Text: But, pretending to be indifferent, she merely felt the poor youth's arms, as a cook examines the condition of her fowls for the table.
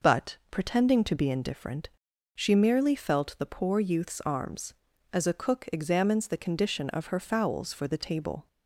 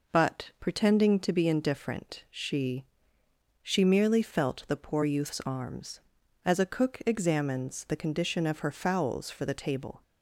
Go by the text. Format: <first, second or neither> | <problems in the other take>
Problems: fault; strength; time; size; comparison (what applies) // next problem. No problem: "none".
first | says "she" twice; at 3.6 s